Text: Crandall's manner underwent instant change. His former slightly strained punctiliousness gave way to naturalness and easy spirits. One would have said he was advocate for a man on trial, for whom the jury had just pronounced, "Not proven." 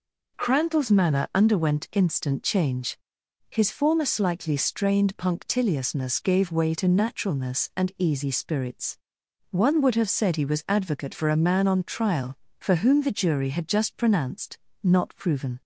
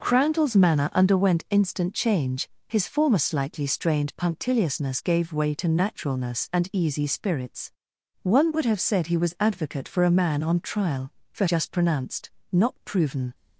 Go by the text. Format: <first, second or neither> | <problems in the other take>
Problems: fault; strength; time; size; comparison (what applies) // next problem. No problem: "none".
first | skips "whom the jury had"; at 11.4 s